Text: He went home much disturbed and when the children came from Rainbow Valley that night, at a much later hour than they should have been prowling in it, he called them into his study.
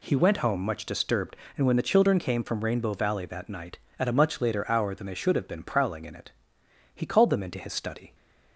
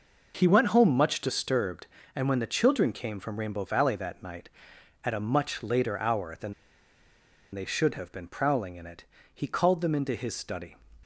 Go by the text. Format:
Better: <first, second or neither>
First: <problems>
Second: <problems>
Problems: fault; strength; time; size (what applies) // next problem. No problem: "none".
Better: first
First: none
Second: pauses between "than" and "they"; at 6.5 s; 1.0 s long